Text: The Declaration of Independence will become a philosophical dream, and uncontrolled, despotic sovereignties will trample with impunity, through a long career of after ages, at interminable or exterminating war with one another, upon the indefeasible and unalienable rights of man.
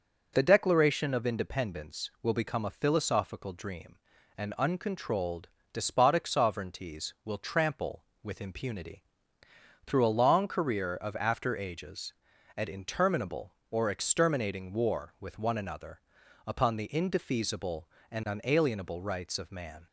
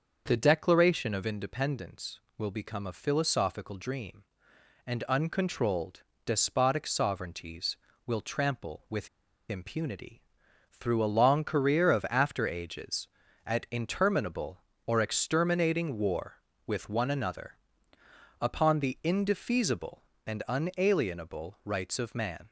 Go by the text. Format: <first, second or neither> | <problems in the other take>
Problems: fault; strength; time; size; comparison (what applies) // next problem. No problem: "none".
first | starts louder than the rest; until 1.2 s; 6.5 dB // pauses between "with" and "impunity"; at 9.0 s; 0.40 s long